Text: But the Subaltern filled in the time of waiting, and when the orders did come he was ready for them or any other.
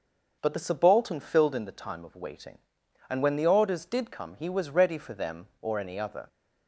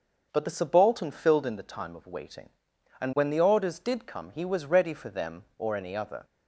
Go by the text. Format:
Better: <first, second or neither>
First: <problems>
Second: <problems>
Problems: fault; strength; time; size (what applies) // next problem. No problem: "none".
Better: neither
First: starts louder than the rest; until 1.4 s; 6 dB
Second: starts louder than the rest; until 1.3 s; 6.5 dB